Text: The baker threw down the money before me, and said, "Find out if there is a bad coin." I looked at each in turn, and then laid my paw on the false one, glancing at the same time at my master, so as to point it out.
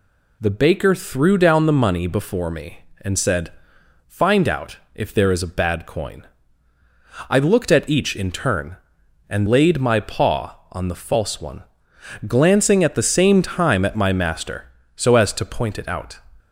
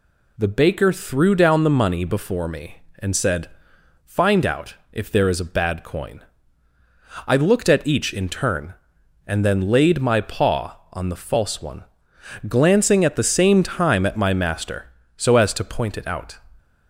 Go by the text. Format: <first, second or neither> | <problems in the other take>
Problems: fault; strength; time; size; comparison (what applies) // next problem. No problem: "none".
second | skips "then"; at 9.4 s